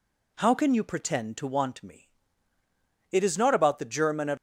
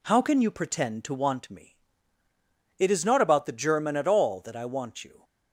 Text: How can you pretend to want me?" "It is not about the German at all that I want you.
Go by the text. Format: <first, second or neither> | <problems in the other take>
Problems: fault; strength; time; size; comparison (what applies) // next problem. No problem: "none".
second | stops before "all that I want you"; at 4.3 s